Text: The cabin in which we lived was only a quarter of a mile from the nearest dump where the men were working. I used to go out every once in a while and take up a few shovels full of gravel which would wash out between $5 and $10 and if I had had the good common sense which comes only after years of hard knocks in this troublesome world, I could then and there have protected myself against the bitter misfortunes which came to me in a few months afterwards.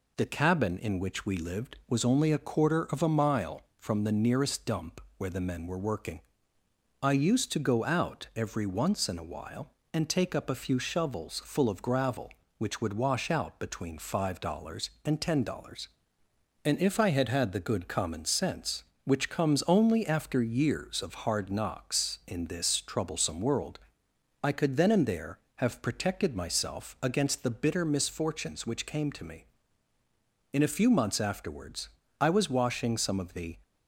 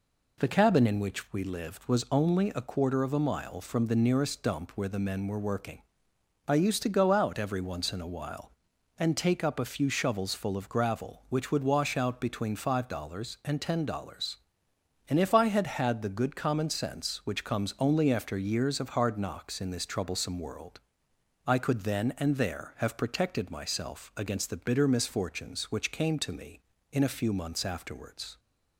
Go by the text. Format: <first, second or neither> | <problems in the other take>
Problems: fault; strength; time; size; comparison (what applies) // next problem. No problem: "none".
second | pauses between "dump" and "where"; slight; at 5.0 s; 0.18 s long // goes on to say "I was washing some of the"; from 32.1 s on; 1.4 s long